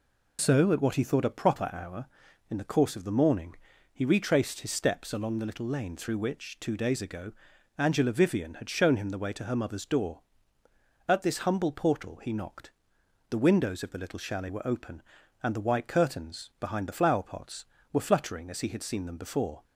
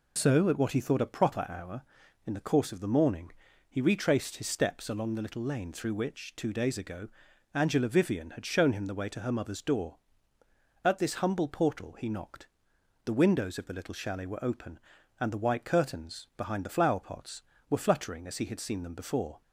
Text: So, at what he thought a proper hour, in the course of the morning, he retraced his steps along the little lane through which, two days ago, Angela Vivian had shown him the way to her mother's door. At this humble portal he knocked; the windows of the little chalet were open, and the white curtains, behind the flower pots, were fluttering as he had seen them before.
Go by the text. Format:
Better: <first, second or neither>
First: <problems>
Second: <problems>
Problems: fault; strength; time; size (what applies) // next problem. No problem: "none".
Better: neither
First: none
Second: none